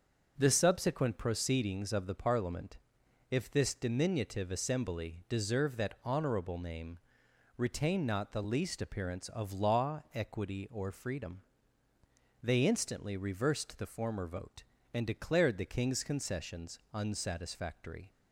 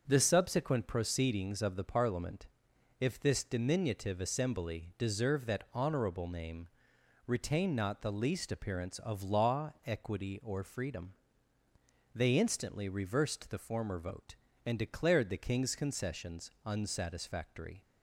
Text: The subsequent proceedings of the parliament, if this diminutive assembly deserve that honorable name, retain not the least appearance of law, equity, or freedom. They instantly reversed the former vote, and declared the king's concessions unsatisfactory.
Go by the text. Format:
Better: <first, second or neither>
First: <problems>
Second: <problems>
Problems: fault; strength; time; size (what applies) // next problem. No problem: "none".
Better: neither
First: starts louder than the rest; until 1.3 s; 6.5 dB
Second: starts louder than the rest; until 1.0 s; 6.5 dB